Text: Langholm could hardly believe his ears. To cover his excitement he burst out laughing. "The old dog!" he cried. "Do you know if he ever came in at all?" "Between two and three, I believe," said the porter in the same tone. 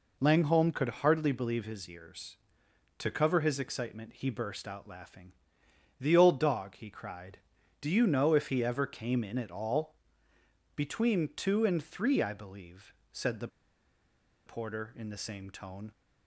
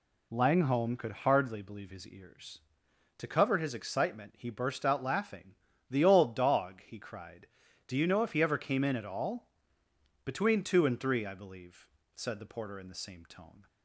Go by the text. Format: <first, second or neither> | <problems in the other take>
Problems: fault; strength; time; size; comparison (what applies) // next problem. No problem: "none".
second | pauses between "the" and "porter"; at 13.4 s; 0.99 s long